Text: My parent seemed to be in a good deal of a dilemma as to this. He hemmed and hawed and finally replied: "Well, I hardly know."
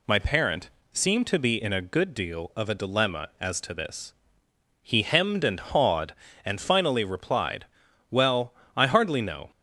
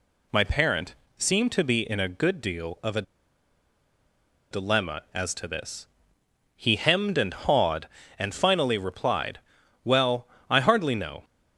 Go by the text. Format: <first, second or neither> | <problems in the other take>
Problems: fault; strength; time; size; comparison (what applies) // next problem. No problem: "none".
first | pauses between "parent" and "seemed"; slight; at 0.9 s; 0.22 s long; slight in the first // pauses between "a" and "dilemma"; strong; at 3.0 s; 1.4 s long